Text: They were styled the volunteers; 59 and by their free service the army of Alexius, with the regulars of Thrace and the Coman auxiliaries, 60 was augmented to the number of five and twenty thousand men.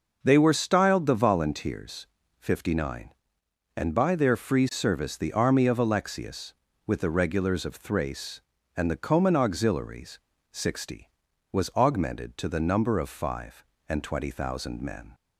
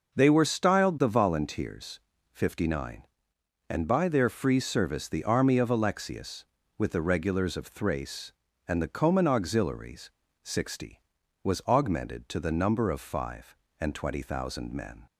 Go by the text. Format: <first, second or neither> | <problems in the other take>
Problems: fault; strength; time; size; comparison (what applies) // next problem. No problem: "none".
neither | none